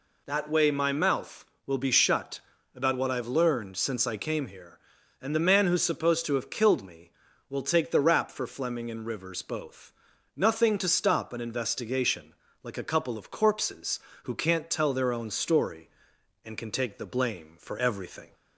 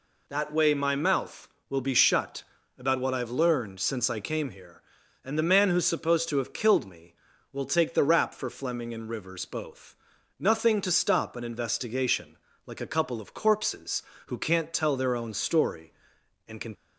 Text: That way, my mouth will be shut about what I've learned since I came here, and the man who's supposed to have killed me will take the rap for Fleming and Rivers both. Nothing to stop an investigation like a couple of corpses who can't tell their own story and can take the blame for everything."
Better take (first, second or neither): first